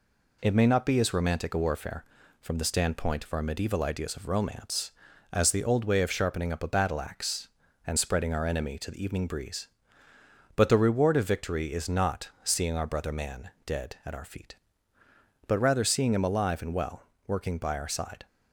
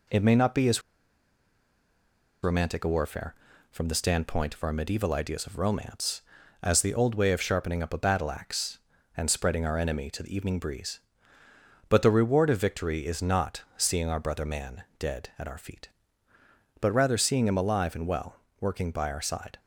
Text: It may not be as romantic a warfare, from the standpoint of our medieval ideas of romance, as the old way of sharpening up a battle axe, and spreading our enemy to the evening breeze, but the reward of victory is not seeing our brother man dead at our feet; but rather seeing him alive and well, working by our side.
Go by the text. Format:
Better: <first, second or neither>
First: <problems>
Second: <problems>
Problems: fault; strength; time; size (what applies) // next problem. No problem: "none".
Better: first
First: pauses between "man" and "dead"; slight; at 13.4 s; 0.16 s long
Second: pauses between "as" and "romantic"; strong; at 0.8 s; 1.6 s long // pauses between "man" and "dead"; slight; at 14.8 s; 0.16 s long